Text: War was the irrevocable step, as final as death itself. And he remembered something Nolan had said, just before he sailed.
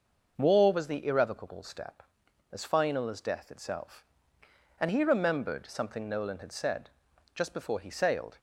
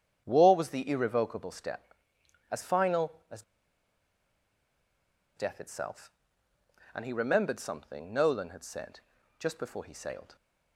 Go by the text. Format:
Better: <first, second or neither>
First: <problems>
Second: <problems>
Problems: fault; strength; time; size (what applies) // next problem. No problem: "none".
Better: first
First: starts louder than the rest; noticeable; until 1.3 s; 6 dB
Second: starts louder than the rest; strong; until 1.2 s; 8.5 dB // pauses between "as" and "death"; strong; at 3.4 s; 1.9 s long